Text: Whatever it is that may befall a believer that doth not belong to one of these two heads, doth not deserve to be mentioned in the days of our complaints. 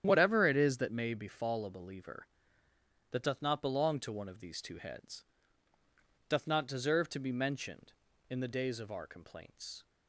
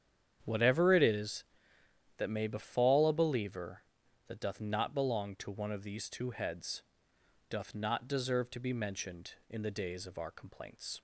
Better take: neither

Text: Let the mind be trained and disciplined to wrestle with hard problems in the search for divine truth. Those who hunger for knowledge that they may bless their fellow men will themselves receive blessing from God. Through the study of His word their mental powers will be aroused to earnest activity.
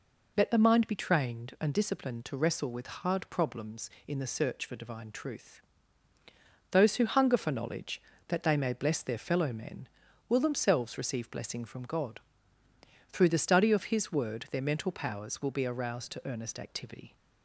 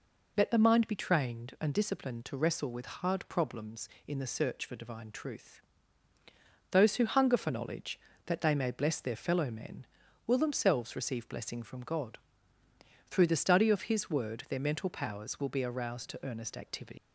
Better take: first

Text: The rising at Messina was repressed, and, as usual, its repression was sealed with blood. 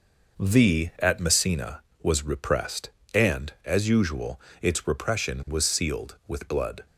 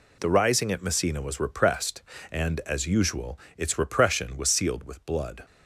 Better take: second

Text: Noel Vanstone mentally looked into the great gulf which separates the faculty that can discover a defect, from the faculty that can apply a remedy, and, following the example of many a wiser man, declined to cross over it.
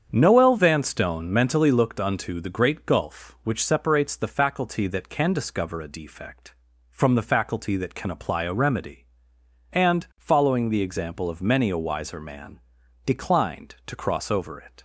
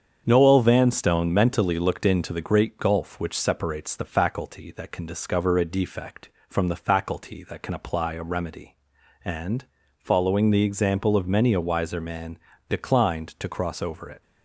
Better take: second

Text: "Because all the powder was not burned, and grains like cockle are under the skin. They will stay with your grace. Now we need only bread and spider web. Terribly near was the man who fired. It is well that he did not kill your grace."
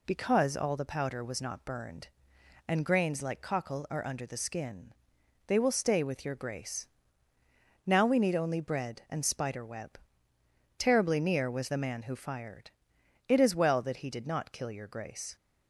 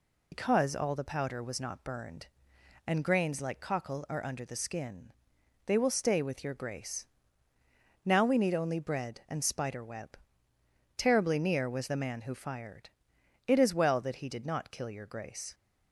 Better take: first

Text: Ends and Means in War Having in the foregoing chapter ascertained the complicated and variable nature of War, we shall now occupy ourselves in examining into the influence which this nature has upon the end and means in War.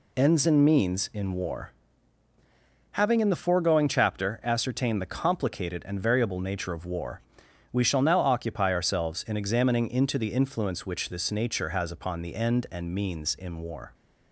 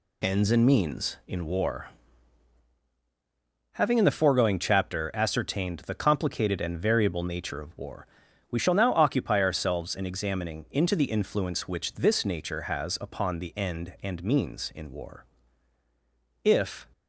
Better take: first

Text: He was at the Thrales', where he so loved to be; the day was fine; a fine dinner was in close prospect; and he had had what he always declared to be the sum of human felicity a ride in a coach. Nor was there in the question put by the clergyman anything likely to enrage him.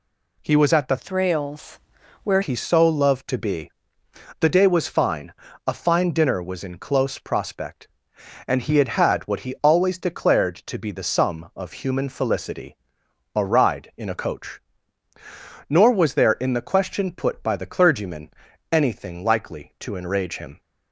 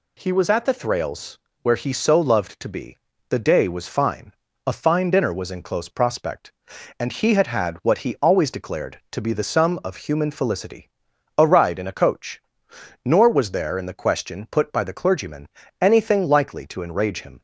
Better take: second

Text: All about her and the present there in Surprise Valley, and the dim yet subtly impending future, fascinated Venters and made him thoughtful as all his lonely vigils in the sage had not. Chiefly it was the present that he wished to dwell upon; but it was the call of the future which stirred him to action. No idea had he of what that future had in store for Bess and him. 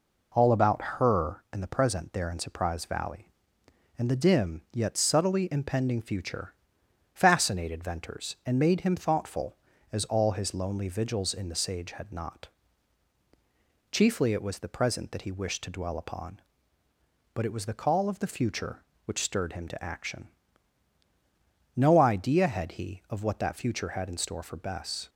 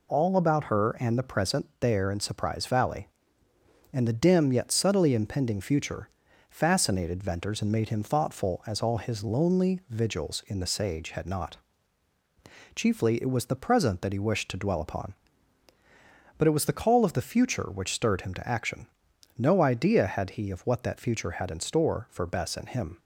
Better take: second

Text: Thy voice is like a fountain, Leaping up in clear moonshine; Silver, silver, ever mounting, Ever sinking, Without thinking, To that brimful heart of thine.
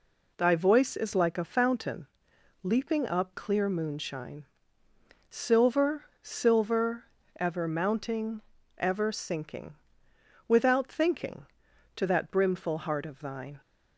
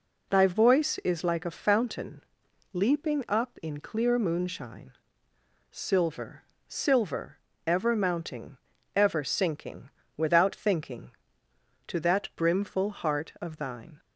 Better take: second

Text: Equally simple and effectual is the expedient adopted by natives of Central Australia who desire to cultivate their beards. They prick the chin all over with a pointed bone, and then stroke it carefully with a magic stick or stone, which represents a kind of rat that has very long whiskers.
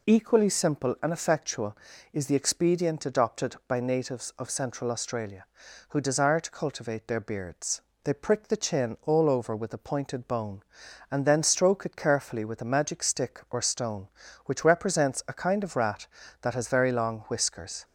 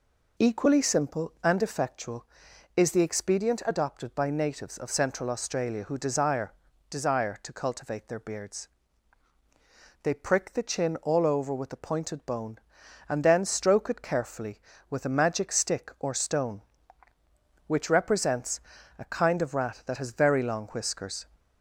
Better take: first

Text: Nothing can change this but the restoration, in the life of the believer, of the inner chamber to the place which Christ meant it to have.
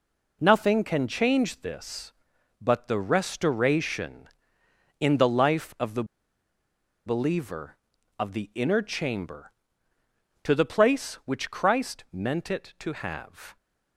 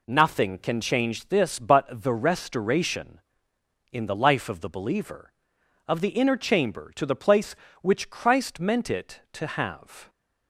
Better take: second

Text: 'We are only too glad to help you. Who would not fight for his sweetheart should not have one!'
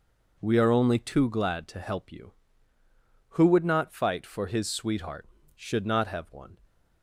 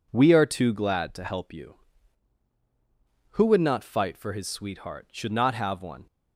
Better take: first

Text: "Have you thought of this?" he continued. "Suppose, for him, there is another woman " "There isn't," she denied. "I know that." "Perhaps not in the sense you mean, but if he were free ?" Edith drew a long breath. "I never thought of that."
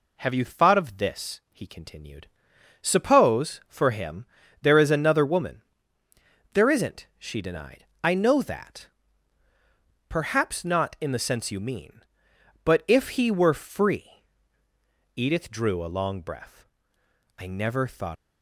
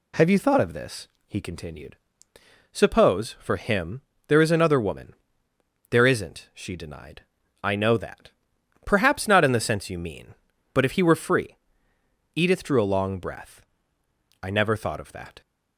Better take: second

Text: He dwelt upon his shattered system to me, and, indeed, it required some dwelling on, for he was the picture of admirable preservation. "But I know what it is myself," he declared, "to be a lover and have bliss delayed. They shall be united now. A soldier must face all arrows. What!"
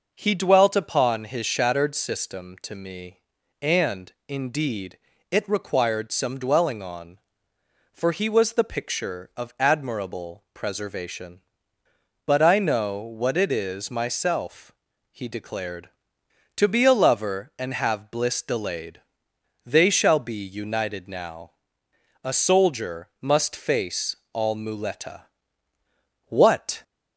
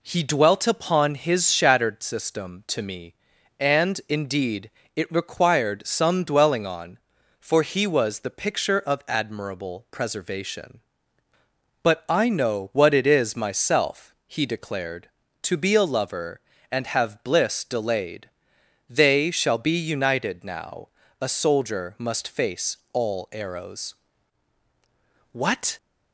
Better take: second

